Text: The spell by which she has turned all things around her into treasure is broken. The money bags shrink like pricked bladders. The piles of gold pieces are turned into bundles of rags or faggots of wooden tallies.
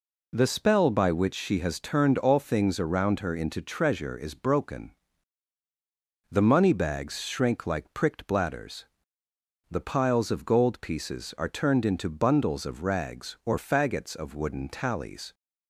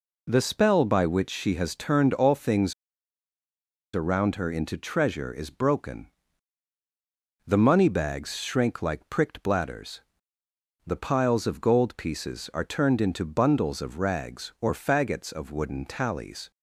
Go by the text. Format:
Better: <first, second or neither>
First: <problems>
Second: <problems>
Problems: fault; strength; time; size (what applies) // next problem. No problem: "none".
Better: first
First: none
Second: pauses between "things" and "around"; at 2.7 s; 1.2 s long